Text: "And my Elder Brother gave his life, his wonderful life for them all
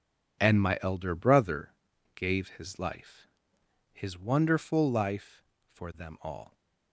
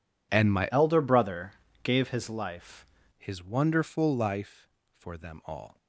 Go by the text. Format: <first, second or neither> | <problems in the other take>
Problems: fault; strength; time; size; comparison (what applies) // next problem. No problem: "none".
first | changes voice from "Elder" to "life"; from 0.7 to 2.8 s; 2.1 s long // pauses between "Brother" and "gave"; slight; at 1.5 s; 0.30 s long; also in the first